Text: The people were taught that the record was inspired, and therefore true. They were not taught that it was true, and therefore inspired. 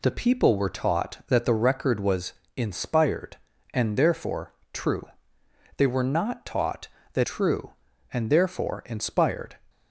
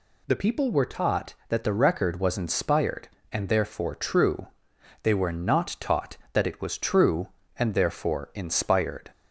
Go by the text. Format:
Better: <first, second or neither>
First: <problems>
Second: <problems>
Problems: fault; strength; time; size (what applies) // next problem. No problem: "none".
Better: second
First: pauses between "was" and "inspired"; slight; at 2.3 s; 0.22 s long // pauses between "therefore" and "true"; slight; at 4.5 s; 0.22 s long // skips "it was"; at 7.2 s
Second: none